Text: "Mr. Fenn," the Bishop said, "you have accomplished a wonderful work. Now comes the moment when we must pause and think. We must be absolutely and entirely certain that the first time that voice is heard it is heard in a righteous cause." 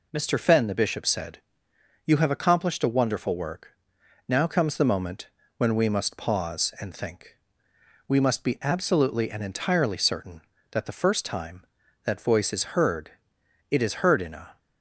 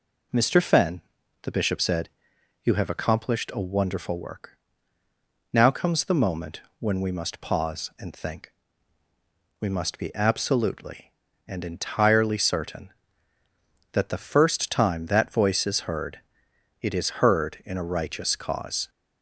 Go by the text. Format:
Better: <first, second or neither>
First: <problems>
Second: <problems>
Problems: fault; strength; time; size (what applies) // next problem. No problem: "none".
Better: second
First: pauses between "moment" and "when"; slight; at 5.2 s; 0.30 s long // pauses between "heard" and "it"; noticeable; at 13.1 s; 0.58 s long // stops before "righteous cause"; at 14.5 s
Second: pauses between "moment" and "when"; slight; at 6.6 s; 0.18 s long // pauses between "heard" and "it"; noticeable; at 16.1 s; 0.62 s long